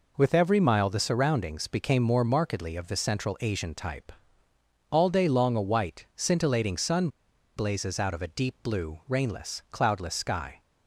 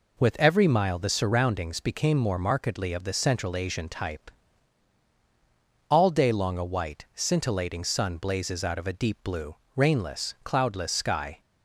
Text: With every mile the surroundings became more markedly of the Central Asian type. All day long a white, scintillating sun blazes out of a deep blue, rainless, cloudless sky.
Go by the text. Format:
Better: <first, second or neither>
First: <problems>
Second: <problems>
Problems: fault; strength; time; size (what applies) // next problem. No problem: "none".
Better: second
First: pauses between "sun" and "blazes"; noticeable; at 7.0 s; 0.48 s long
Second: none